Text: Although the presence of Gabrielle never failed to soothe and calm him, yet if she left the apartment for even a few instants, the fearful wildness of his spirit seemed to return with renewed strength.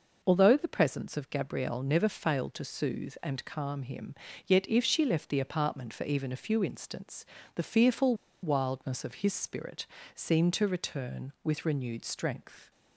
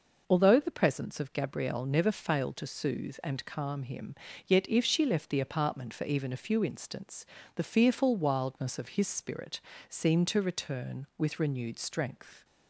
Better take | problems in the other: second | pauses between "fearful" and "wildness"; slight; at 8.1 s; 0.28 s long // pauses between "spirit" and "seemed"; slight; at 9.8 s; 0.30 s long; slight in the second

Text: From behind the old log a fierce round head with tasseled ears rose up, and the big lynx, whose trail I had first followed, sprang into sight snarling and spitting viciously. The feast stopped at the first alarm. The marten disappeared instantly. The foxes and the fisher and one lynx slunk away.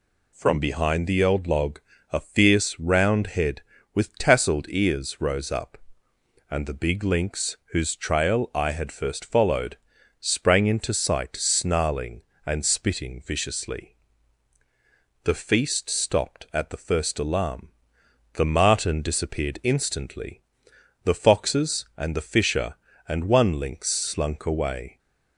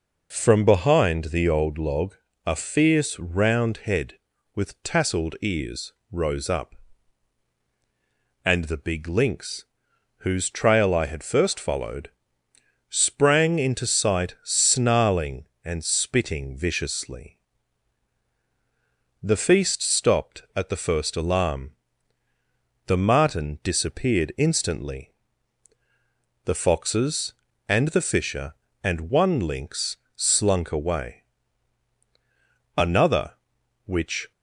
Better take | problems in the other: first | pauses between "log" and "a"; slight; at 2.1 s; 0.32 s long; slight in the first // pauses between "ears" and "rose"; slight; at 5.9 s; 0.18 s long // pauses between "lynx" and "slunk"; slight; at 29.9 s; 0.26 s long // goes on to say "Another which"; from 32.7 s on; 1.5 s long

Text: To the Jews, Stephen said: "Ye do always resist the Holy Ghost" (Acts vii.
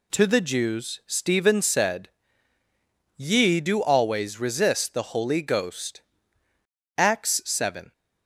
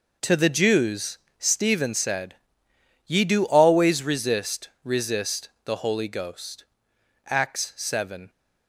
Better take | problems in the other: first | says "resist" twice; at 4.8 s

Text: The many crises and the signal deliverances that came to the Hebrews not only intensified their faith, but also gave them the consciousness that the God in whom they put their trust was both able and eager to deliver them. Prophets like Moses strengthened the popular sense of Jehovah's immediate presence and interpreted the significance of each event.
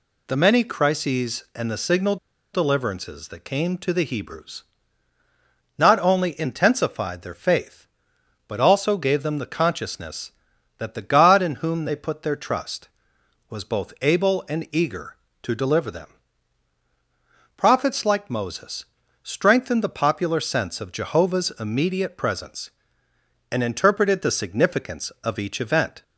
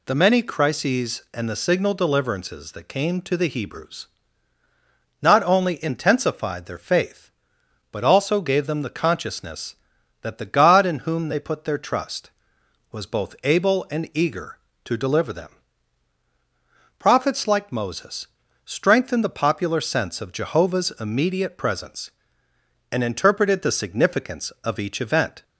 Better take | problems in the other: second | pauses between "signal" and "deliverances"; at 2.1 s; 0.37 s long // pauses between "Hebrews" and "not"; at 4.6 s; 1.1 s long; also in the second // pauses between "Moses" and "strengthened"; at 18.8 s; 0.38 s long; also in the second

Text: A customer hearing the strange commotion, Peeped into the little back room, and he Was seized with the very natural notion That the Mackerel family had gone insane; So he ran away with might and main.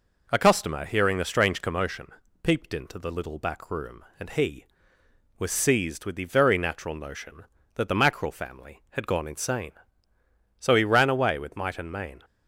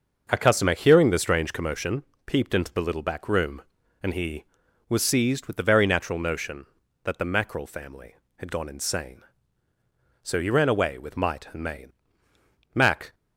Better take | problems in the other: first | starts louder than the rest; until 1.3 s; 6 dB // goes on to say "Mac"; slight; from 12.7 s on; 0.40 s long

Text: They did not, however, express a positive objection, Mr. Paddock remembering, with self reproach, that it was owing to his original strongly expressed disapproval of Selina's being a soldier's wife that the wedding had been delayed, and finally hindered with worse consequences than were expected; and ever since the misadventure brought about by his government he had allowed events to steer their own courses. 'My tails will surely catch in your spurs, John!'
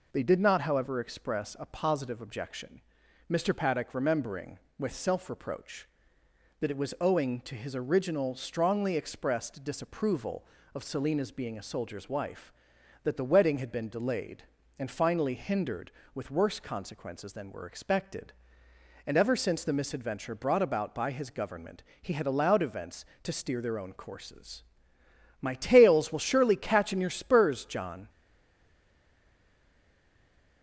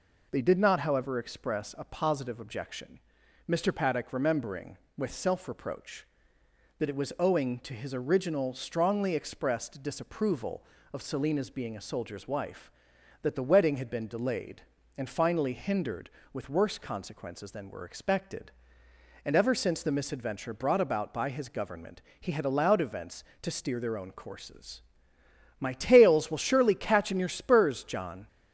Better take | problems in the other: second | pauses between "government" and "he"; slight; at 21.8 s; 0.18 s long; slight in the second // stays silent after the last word; strong; from 28.0 s on; 2.6 s long

